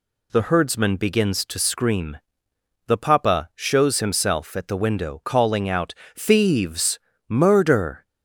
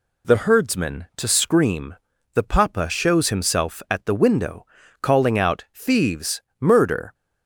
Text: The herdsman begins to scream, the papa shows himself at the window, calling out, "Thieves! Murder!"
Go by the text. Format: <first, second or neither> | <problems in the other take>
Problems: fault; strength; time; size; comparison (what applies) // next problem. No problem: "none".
first | skips "begins"; at 1.1 s